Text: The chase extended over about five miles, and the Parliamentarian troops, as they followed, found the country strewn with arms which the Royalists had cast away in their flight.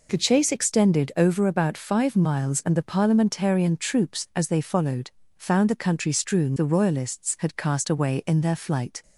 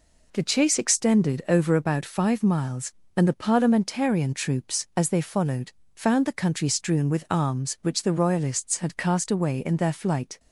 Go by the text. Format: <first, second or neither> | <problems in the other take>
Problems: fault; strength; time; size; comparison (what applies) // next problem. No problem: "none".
second | skips "with arms which"; at 6.5 s